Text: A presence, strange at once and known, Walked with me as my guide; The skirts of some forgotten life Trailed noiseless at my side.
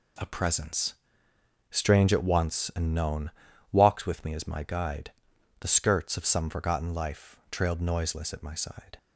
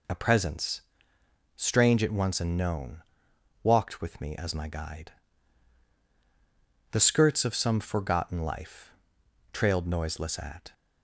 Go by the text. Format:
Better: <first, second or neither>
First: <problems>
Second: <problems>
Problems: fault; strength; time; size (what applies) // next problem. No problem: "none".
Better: first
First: pauses between "life" and "Trailed"; slight; at 7.3 s; 0.16 s long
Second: pauses between "life" and "Trailed"; noticeable; at 8.9 s; 0.58 s long // stops before "my side"; at 10.7 s